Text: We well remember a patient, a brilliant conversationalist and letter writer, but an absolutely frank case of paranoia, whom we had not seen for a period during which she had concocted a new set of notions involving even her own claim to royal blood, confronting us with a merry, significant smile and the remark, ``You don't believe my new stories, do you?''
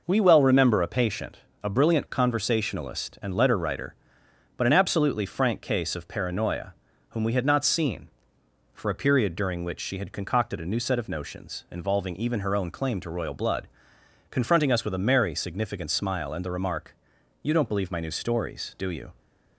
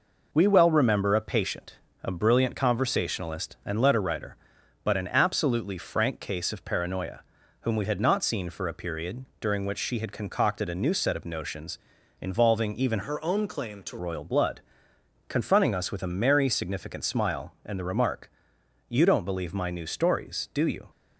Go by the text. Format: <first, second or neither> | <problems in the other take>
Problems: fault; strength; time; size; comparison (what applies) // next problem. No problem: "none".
first | pauses between "period" and "during"; slight; at 9.2 s; 0.16 s long // pauses between "notions" and "involving"; at 11.7 s; 0.44 s long // changes voice from "her" to "to"; from 13.0 to 13.9 s; 0.9 s long